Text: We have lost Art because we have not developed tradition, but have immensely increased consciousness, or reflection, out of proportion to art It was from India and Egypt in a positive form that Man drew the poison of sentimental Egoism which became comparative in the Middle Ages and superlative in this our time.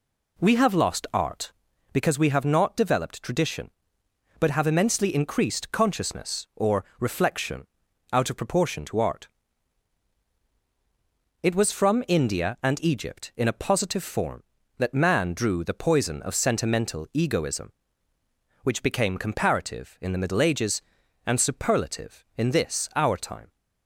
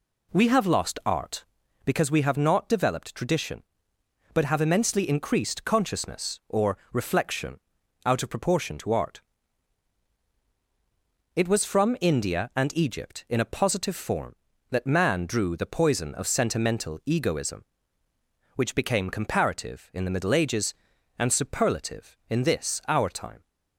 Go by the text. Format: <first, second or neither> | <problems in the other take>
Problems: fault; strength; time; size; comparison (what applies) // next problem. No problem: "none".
neither | pauses between "or" and "reflection"; slight; the same in both // pauses between "art" and "It"; strong; the same in both